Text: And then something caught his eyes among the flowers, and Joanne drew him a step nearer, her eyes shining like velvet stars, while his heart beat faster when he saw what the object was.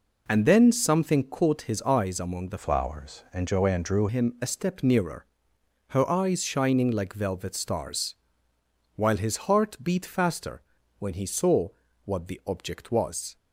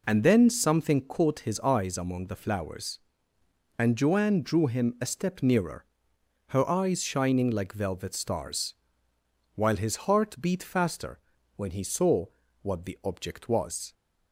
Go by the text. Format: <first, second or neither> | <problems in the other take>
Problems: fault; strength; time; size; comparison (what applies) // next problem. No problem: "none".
second | changes voice from "flowers" to "drew"; from 2.5 to 4.0 s; 1.5 s long // pauses between "faster" and "when"; slight; at 10.6 s; 0.36 s long; slight in the second // pauses between "saw" and "what"; at 11.6 s; 0.38 s long; also in the second